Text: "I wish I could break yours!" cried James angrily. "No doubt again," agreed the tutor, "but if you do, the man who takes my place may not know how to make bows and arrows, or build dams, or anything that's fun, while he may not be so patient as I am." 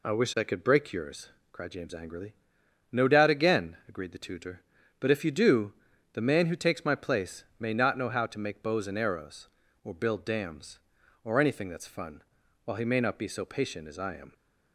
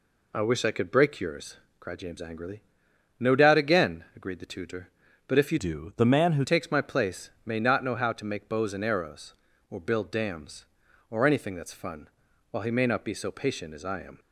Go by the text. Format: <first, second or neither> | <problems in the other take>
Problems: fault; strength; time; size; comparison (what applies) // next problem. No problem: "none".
first | changes voice from "do" to "who"; from 5.5 to 6.4 s; 0.9 s long // pauses between "place" and "may"; slight; at 7.2 s; 0.16 s long; slight in the first